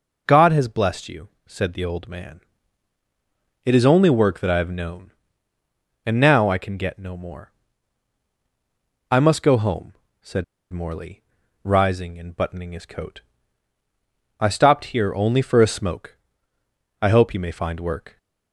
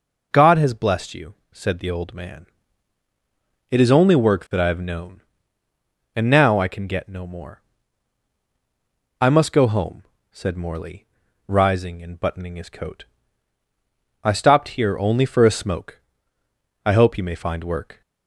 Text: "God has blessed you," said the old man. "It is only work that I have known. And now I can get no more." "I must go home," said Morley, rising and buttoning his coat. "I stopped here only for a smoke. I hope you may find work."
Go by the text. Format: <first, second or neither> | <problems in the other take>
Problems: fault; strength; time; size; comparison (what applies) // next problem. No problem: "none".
second | pauses between "said" and "Morley"; slight; at 10.4 s; 0.29 s long